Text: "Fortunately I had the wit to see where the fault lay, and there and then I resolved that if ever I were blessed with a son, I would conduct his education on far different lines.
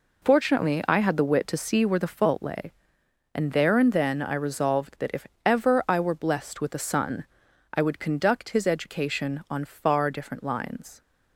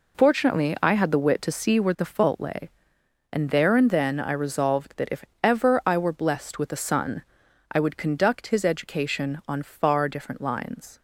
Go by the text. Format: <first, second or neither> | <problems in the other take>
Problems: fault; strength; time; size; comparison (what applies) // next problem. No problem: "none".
neither | pauses between "if" and "ever"; slight; the same in both